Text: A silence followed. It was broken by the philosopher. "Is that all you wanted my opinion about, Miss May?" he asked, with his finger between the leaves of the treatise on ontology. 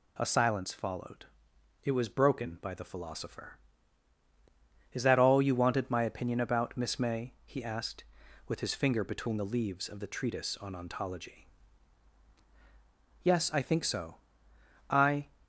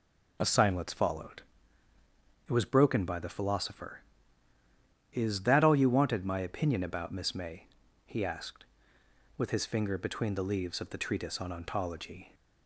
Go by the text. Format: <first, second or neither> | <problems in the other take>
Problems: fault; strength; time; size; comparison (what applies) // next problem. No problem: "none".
second | goes on to say "Yes I think so I"; strong; from 13.2 s on; 2.0 s long